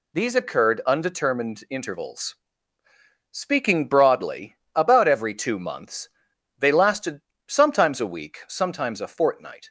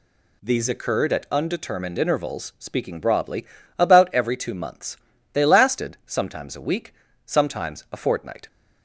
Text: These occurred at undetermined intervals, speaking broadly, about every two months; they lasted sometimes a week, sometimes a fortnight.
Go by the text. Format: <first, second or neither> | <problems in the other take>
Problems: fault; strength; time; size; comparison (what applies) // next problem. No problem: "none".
second | skips "at"; at 0.8 s // pauses between "lasted" and "sometimes"; slight; at 7.2 s; 0.26 s long